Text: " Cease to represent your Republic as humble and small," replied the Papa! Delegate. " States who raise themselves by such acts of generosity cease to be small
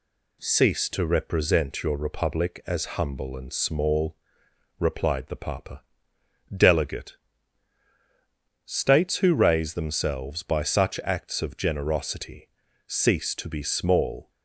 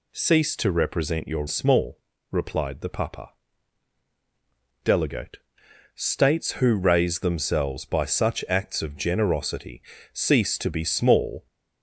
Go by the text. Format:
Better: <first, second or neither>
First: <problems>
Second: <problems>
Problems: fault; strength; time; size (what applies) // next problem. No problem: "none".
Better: first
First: pauses between "generosity" and "cease"; at 12.4 s; 0.40 s long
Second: skips "Republic as humble and"; at 1.4 s // pauses between "generosity" and "cease"; slight; at 9.8 s; 0.34 s long